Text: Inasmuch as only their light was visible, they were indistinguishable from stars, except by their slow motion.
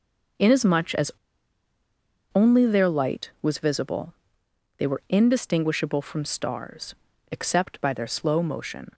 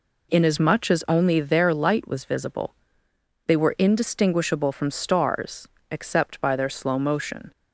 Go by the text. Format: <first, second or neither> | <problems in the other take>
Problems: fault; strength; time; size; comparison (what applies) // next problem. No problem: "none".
second | pauses between "as" and "only"; at 1.1 s; 1.2 s long